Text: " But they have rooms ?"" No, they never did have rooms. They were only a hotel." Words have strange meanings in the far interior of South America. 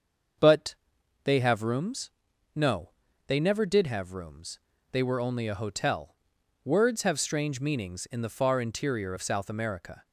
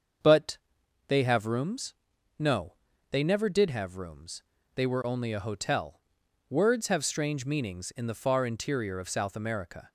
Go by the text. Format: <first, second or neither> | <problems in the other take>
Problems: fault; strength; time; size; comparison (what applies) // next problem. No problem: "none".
neither | starts louder than the rest; the same in both // pauses between "But" and "they"; noticeable; the same in both